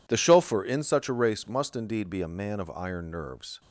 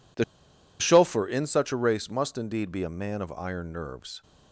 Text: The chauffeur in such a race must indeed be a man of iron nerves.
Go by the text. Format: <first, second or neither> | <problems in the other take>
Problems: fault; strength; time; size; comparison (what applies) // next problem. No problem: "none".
first | pauses between "The" and "chauffeur"; noticeable; at 0.2 s; 0.57 s long